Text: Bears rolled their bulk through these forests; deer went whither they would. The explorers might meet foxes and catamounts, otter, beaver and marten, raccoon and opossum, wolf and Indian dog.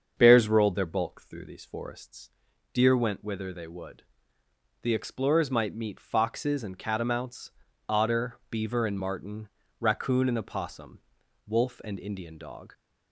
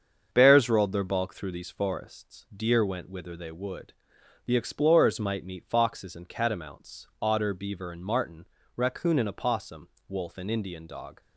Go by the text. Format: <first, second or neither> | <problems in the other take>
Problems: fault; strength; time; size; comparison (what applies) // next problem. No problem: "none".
neither | starts louder than the rest; the same in both